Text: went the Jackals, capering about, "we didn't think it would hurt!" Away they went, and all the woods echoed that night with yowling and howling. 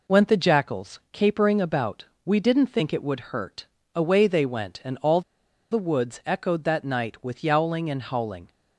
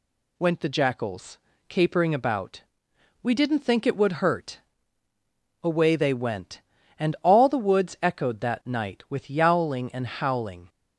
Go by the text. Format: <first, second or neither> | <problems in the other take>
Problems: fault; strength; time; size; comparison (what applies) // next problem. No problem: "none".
second | pauses between "all" and "the"; noticeable; at 5.2 s; 0.50 s long